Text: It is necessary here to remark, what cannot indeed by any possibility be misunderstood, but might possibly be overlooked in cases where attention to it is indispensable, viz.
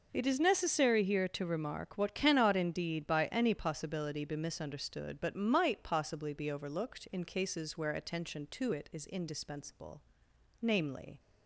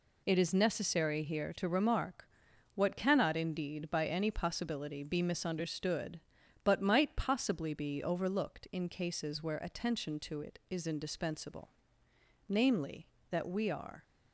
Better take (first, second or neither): first